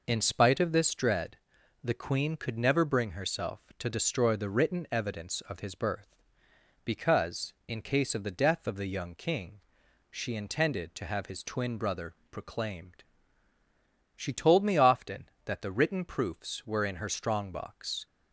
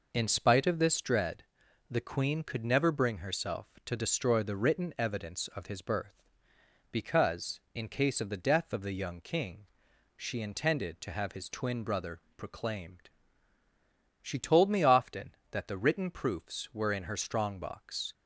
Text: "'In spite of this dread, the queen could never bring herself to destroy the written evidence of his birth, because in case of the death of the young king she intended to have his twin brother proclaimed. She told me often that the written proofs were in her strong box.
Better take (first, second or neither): neither